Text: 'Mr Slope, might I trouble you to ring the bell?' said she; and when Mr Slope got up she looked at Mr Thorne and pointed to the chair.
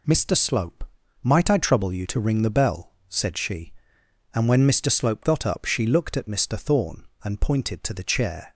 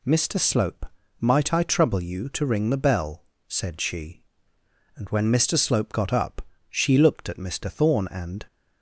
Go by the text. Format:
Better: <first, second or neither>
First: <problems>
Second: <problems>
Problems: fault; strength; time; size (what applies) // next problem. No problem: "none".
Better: first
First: none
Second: pauses between "up" and "she"; slight; at 6.4 s; 0.30 s long // stops before "pointed to the chair"; at 8.4 s